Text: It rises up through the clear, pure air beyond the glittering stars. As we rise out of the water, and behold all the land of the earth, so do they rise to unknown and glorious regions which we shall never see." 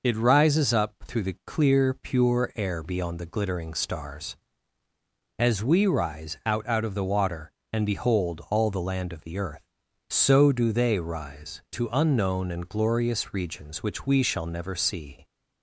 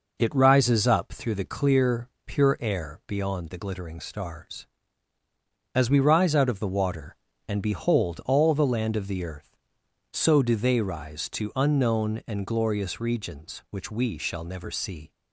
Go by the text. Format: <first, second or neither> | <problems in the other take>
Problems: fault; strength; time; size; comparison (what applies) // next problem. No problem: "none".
second | says "out" twice; at 6.6 s